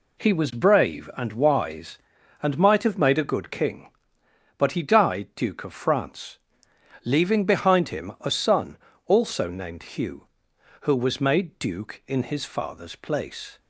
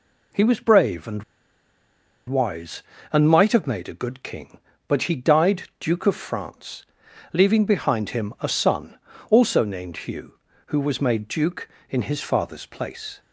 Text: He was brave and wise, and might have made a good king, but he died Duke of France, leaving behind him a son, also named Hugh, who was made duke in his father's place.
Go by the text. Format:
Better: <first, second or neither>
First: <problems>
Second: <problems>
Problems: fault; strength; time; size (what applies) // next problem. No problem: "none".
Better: first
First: none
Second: pauses between "and" and "wise"; at 1.2 s; 1.0 s long // pauses between "died" and "Duke"; slight; at 5.6 s; 0.16 s long